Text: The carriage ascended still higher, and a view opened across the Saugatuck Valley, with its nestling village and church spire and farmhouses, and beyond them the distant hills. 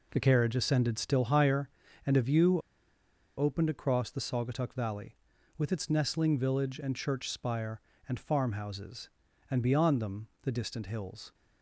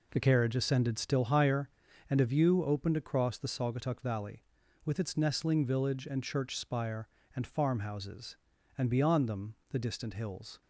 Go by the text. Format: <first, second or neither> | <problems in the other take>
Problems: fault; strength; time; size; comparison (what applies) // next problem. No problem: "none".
second | pauses between "view" and "opened"; noticeable; at 2.5 s; 0.78 s long